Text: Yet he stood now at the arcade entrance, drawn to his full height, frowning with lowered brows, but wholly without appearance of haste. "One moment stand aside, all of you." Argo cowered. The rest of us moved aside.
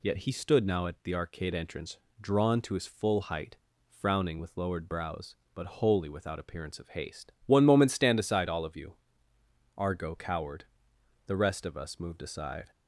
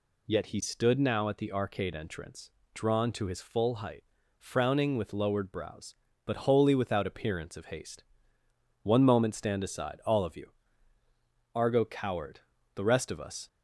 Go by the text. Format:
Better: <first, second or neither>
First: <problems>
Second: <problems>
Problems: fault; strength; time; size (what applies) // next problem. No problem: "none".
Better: first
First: none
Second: stops before "moved aside"; at 13.4 s